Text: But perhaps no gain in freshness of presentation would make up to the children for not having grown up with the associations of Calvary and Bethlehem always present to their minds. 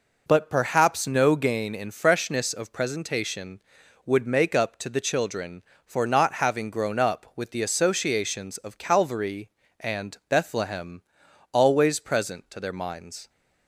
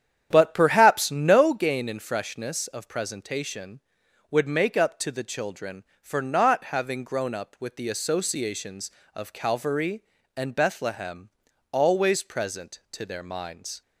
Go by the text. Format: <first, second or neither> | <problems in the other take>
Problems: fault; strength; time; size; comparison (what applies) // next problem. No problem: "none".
first | starts louder than the rest; strong; until 1.5 s; 9.5 dB // pauses between "Bethlehem" and "always"; at 11.2 s; 0.44 s long; noticeable in the first